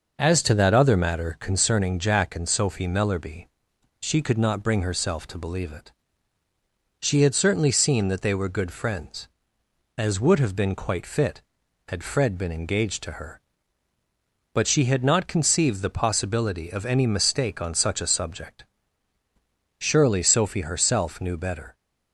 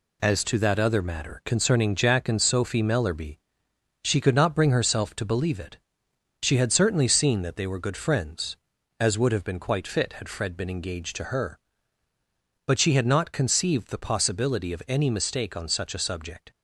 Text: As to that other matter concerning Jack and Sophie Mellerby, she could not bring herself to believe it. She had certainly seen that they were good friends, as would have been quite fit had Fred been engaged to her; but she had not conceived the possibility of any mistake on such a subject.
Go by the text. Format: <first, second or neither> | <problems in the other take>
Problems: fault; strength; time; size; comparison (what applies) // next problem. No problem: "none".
second | goes on to say "Surely Sophie herself knew better"; strong; from 19.8 s on; 1.9 s long